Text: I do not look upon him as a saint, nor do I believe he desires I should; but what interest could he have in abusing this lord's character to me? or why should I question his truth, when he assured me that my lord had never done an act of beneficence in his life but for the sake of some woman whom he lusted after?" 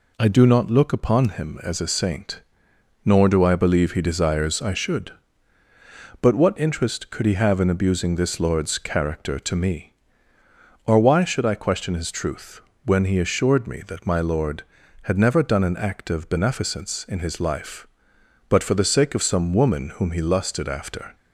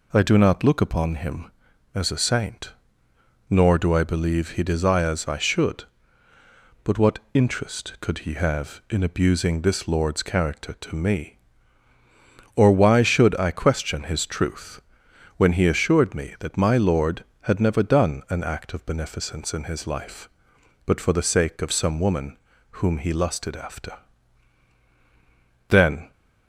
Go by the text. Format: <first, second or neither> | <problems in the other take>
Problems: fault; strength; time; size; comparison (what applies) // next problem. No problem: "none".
first | pauses between "woman" and "whom"; slight; at 22.3 s; 0.36 s long // goes on to say "Then"; slight; from 25.6 s on; 0.42 s long